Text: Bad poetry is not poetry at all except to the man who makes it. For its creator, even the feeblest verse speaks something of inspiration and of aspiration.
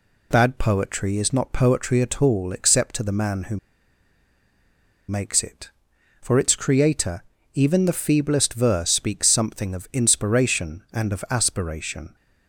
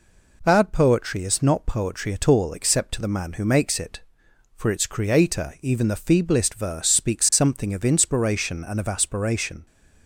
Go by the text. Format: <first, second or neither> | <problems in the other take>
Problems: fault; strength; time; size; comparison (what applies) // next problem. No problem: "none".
second | pauses between "who" and "makes"; strong; at 3.5 s; 1.5 s long